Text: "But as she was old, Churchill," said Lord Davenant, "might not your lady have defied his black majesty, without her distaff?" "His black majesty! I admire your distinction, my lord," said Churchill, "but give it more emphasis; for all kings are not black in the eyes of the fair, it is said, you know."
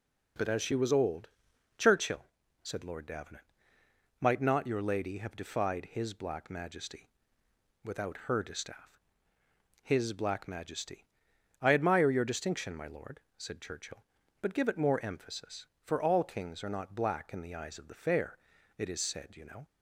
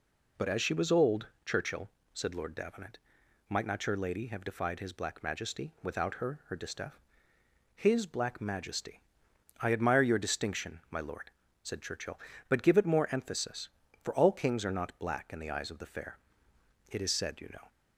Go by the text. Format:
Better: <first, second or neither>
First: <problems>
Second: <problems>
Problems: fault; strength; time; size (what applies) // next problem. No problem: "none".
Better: first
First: none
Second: says "her" twice; at 6.4 s